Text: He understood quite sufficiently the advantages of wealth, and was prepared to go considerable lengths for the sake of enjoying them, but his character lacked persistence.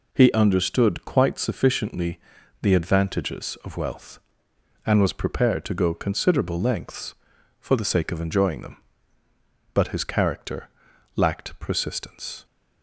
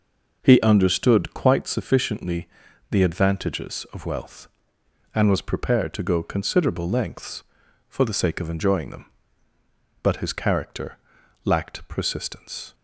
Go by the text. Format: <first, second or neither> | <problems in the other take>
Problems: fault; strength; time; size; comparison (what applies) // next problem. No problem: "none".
first | starts louder than the rest; noticeable; until 1.7 s; 5.5 dB // pauses between "sufficiently" and "the"; at 2.4 s; 0.42 s long; also in the first // pauses between "character" and "lacked"; noticeable; at 10.9 s; 0.48 s long; noticeable in the first